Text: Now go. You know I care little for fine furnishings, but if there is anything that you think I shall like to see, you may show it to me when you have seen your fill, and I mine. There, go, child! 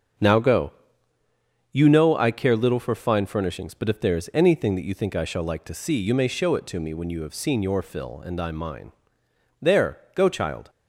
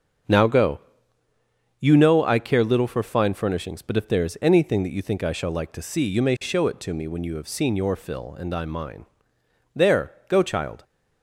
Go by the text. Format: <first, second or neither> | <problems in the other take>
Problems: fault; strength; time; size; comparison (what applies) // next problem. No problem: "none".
neither | starts louder than the rest; the same in both